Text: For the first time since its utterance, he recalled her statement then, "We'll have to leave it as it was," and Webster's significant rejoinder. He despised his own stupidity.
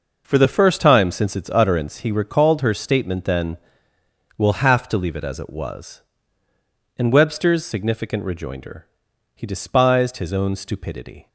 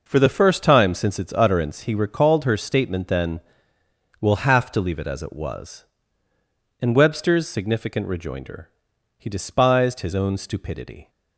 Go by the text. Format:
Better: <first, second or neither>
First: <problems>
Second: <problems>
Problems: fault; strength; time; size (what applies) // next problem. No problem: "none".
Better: neither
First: none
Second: none